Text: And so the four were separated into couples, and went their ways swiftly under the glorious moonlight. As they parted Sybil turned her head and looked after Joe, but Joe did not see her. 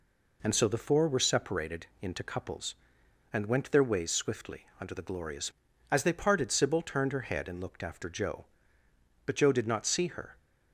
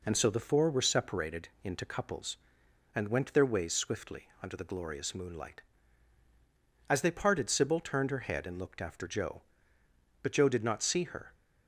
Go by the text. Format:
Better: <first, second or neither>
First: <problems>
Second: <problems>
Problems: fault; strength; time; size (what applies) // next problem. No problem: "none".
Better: second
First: skips "moonlight"; at 5.7 s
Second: none